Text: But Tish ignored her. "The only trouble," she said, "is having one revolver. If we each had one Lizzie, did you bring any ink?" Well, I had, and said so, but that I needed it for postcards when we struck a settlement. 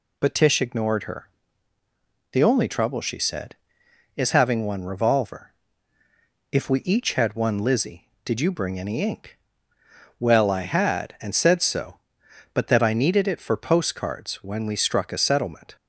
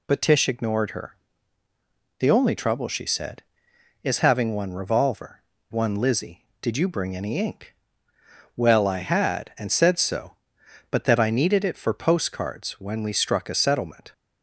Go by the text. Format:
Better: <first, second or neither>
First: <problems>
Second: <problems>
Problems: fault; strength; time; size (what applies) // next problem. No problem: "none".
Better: first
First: none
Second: skips "If we each had"; at 5.5 s